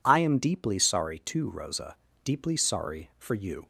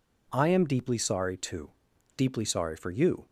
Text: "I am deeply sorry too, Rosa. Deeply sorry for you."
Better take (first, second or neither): first